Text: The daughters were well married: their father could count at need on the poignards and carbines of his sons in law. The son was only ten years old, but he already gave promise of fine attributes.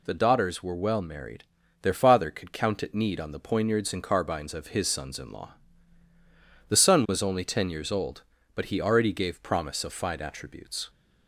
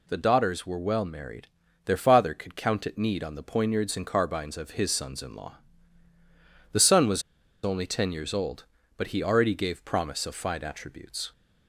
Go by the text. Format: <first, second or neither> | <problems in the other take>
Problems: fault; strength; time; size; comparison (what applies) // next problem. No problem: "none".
first | pauses between "was" and "only"; at 7.2 s; 0.41 s long